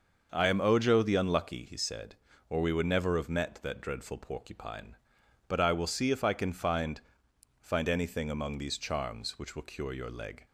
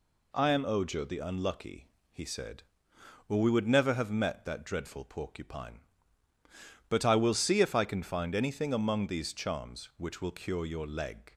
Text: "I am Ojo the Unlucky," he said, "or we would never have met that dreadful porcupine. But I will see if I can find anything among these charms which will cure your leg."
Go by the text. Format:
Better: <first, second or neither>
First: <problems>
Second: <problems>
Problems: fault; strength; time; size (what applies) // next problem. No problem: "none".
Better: second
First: starts louder than the rest; noticeable; until 1.3 s; 6 dB // says "find" twice; at 7.5 s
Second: none